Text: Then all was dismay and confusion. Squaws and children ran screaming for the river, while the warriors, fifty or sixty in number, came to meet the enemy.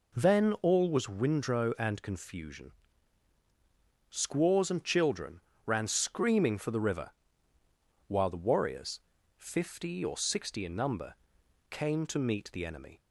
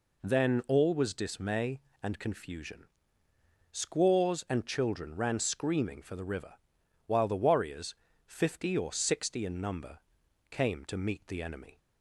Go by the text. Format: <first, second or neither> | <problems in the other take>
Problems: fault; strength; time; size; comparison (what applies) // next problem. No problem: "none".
second | says "windrow" for "dismay"; at 1.0 s // pauses between "children" and "ran"; slight; at 5.3 s; 0.26 s long